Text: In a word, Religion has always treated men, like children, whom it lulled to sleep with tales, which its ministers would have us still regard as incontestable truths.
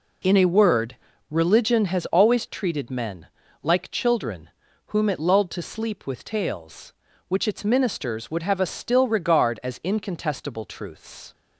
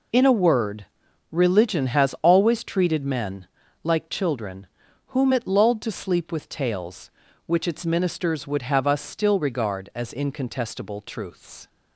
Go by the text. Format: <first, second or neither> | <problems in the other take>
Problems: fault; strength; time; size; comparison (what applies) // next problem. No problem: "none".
neither | none